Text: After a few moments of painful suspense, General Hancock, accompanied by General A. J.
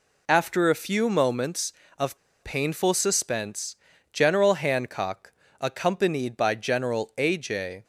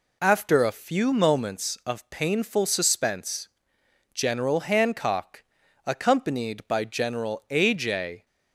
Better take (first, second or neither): second